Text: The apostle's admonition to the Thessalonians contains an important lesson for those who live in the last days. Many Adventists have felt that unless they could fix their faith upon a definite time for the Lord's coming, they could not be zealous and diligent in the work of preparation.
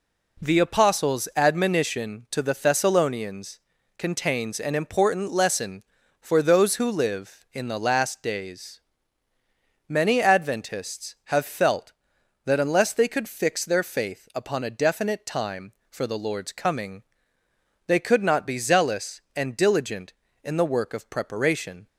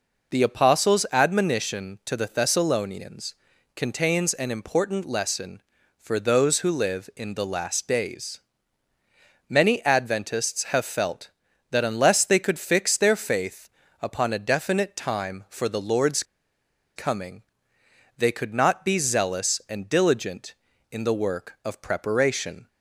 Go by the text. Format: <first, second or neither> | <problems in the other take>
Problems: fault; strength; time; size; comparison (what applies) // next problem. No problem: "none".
first | pauses between "Thessalonians" and "contains"; at 3.3 s; 0.40 s long; also in the first // pauses between "faith" and "upon"; slight; at 13.6 s; 0.32 s long // pauses between "Lord's" and "coming"; noticeable; at 16.2 s; 0.72 s long